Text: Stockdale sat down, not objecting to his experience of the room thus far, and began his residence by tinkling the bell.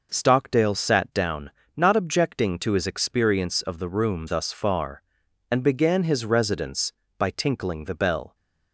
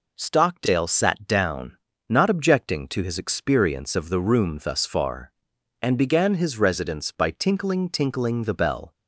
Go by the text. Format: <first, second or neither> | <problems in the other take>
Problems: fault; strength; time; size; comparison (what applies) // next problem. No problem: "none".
first | says "tinkling" twice; at 7.8 s